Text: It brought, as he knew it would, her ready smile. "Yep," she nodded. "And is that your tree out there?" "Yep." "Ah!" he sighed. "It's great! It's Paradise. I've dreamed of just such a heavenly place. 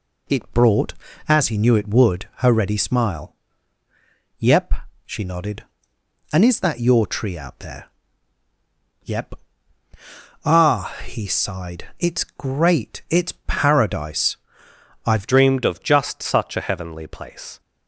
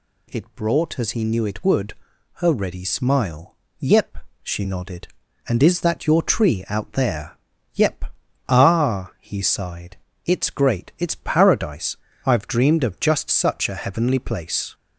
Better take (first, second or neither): second